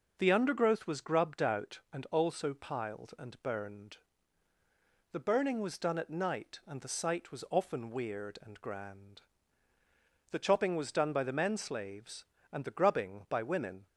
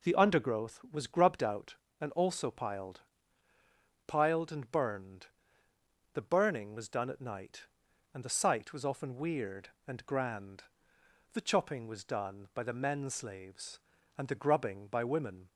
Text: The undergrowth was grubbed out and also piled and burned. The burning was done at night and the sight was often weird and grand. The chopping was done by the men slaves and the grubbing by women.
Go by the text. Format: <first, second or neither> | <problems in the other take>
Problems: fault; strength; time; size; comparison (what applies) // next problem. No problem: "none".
first | says "piled" twice; at 4.0 s